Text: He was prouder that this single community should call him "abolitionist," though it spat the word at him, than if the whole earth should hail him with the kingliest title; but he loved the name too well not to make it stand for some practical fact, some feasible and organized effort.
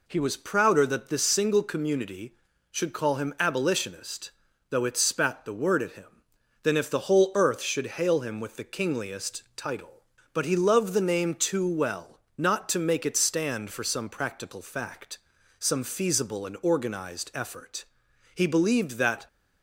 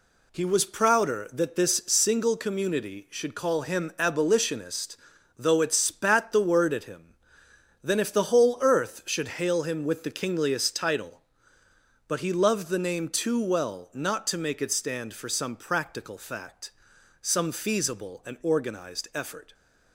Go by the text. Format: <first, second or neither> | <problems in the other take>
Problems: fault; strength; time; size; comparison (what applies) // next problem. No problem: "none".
second | pauses between "well" and "not"; slight; at 12.2 s; 0.16 s long // goes on to say "He believed that"; noticeable; from 18.3 s on; 0.94 s long